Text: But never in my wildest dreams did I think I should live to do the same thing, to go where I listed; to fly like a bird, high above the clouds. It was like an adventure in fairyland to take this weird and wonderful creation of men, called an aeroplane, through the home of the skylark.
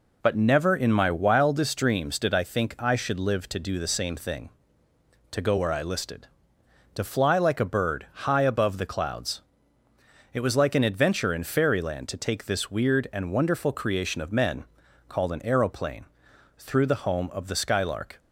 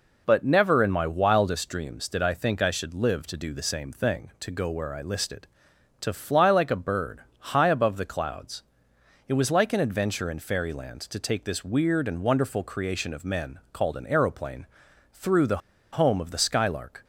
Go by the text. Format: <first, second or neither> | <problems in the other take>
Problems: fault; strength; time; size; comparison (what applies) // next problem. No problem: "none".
first | pauses between "the" and "home"; slight; at 15.5 s; 0.35 s long